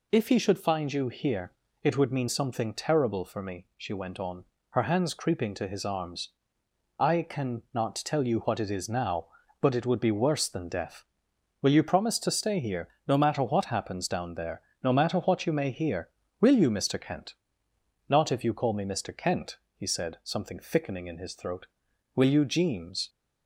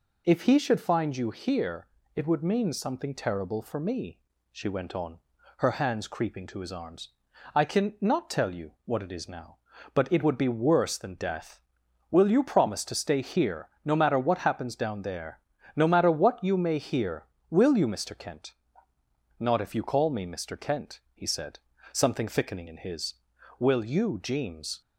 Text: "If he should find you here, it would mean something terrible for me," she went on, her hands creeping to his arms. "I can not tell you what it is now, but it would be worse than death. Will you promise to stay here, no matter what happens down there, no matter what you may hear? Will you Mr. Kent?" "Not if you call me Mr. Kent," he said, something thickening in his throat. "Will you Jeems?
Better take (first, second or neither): first